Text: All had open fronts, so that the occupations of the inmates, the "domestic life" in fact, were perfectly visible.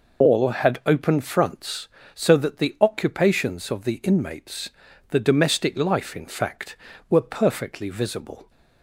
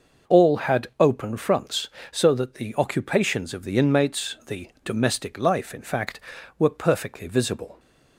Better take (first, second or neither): second